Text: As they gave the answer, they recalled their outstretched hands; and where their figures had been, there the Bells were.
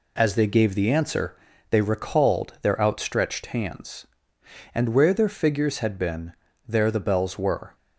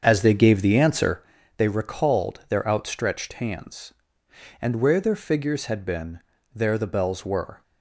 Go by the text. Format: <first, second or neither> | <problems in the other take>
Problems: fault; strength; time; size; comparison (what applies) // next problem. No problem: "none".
first | starts louder than the rest; strong; until 1.2 s; 7 dB